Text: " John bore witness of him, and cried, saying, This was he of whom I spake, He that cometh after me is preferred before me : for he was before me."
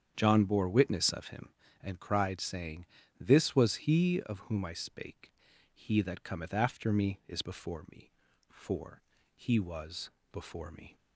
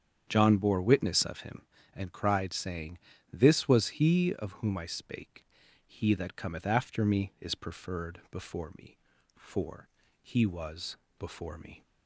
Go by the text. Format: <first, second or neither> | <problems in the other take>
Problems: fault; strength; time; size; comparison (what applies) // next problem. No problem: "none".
second | starts louder than the rest; strong; until 1.1 s; 8 dB; strong in the second // skips "preferred"; at 7.4 s // pauses between "for" and "he"; slight; at 9.0 s; 0.34 s long; slight in the second // pauses between "was" and "before"; slight; at 10.1 s; 0.20 s long; slight in the second